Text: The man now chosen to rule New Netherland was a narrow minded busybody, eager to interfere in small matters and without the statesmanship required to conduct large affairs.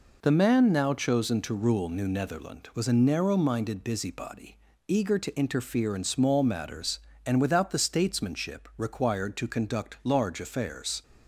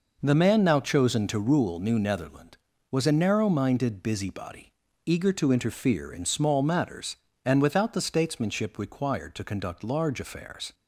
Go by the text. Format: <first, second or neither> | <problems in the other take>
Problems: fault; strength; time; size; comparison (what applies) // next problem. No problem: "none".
neither | none